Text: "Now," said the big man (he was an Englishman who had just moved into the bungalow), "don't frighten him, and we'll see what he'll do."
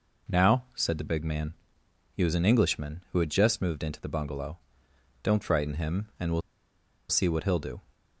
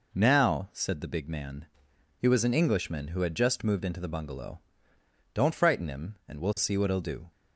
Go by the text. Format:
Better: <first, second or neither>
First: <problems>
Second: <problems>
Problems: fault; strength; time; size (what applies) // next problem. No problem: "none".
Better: second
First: pauses between "we'll" and "see"; noticeable; at 6.4 s; 0.68 s long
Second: none